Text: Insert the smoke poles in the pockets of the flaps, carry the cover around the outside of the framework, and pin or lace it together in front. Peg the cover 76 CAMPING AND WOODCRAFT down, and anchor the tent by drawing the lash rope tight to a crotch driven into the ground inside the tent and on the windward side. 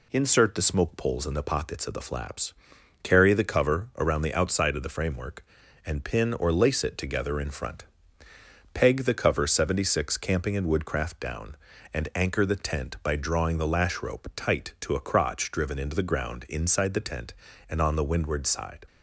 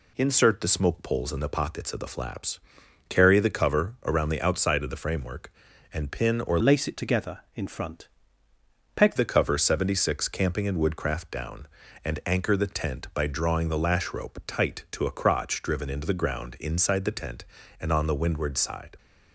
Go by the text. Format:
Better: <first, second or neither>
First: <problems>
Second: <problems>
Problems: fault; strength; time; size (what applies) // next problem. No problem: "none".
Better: first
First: none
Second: changes voice from "lace" to "Peg"; from 6.6 to 9.1 s; 2.5 s long